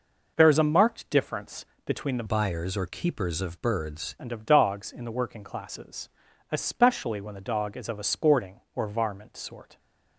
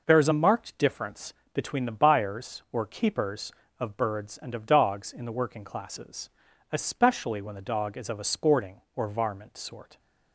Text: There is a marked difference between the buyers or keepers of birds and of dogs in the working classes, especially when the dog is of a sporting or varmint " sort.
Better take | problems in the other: second | pauses between "difference" and "between"; slight; at 1.6 s; 0.18 s long; slight in the second // changes voice from "buyers" to "birds"; from 2.2 to 4.1 s; 1.9 s long

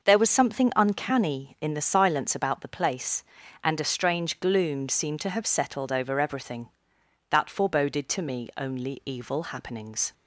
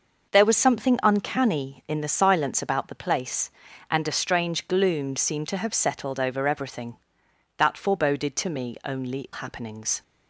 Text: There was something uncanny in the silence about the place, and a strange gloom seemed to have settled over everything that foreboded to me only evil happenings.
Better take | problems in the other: first | skips "evil"; at 9.3 s

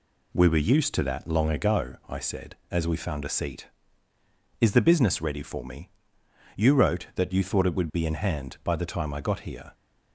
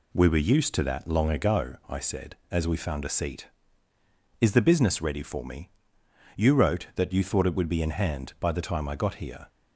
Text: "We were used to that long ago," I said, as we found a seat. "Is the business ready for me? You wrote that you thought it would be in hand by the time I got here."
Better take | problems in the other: neither | none

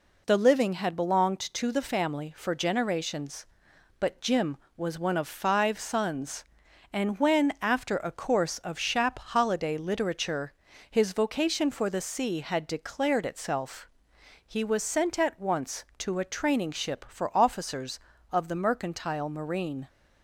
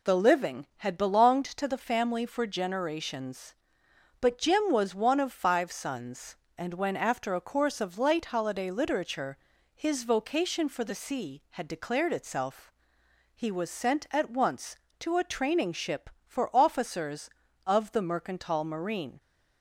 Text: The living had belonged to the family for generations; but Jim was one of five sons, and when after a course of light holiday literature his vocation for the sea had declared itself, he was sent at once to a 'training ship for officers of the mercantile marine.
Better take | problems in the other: second | says "shap" for "light"; at 8.7 s // pauses between "literature" and "his"; slight; at 10.5 s; 0.36 s long; also in the second

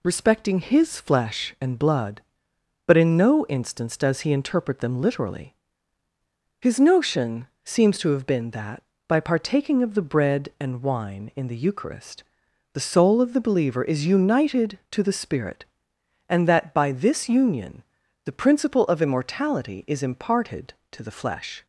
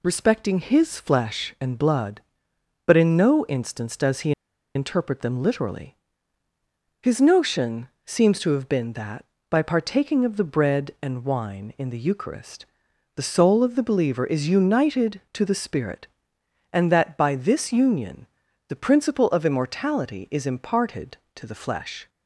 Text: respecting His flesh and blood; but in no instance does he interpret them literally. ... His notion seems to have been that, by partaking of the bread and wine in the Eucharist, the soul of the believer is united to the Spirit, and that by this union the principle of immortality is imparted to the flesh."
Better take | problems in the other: first | pauses between "he" and "interpret"; at 4.3 s; 0.44 s long // pauses between "notion" and "seems"; slight; at 7.8 s; 0.16 s long; slight in the first // pauses between "union" and "the"; at 18.2 s; 0.42 s long; also in the first

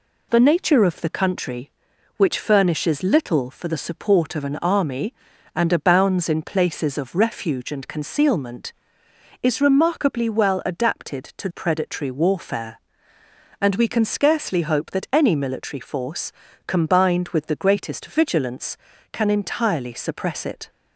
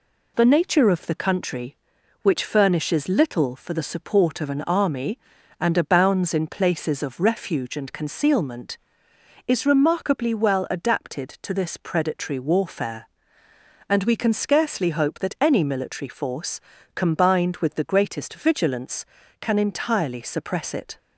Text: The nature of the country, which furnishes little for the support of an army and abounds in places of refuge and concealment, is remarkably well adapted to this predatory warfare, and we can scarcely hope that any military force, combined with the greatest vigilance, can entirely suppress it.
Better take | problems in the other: second | skips "this"; at 11.4 s

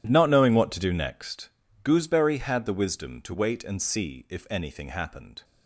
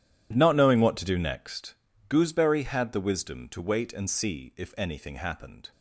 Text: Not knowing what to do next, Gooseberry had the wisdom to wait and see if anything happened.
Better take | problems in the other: neither | none

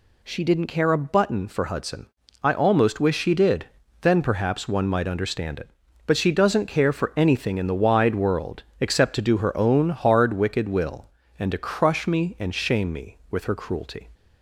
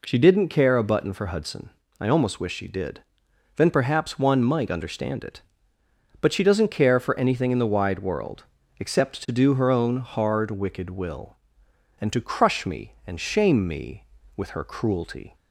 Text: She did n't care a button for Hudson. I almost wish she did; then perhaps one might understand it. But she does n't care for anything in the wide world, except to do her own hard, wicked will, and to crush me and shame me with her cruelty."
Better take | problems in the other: neither | none

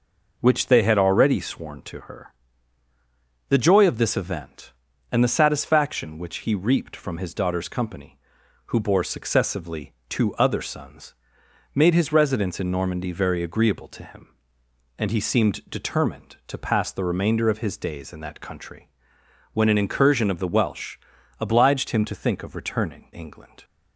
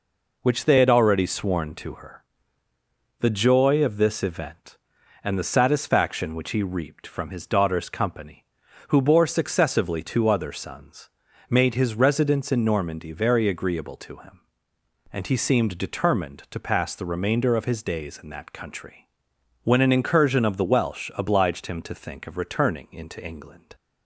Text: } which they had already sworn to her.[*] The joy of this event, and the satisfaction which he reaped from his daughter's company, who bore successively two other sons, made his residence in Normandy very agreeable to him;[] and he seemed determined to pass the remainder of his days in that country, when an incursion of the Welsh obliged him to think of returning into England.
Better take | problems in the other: second | pauses between "successively" and "two"; slight; at 9.9 s; 0.16 s long // pauses between "Welsh" and "obliged"; at 20.9 s; 0.42 s long // skips "into"; at 23.1 s

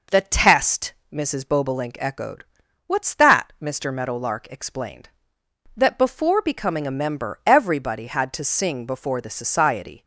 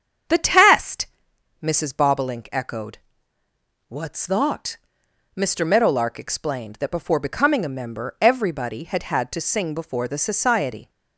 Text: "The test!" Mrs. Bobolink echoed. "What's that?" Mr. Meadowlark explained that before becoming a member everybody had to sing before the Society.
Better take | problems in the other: first | starts louder than the rest; strong; until 1.8 s; 8 dB // says "had" twice; at 9.0 s

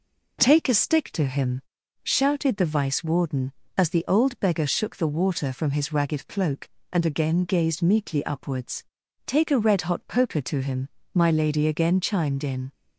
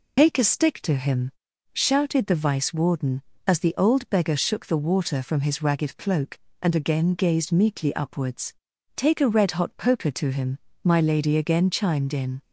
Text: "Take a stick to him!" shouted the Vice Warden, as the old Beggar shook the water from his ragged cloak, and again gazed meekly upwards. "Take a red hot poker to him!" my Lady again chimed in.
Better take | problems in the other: first | loses the start of "Take"; at 0.1 s; 90 ms

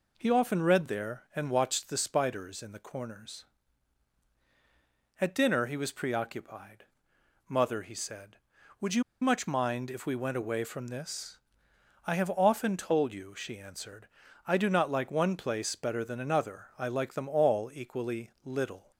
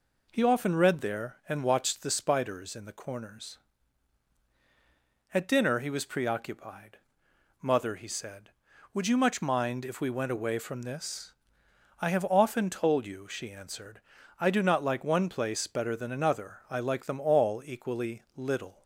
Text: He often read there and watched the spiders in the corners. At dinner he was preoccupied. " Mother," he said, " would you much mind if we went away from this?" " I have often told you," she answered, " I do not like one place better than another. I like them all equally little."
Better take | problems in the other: second | pauses between "you" and "much"; slight; at 9.0 s; 0.19 s long

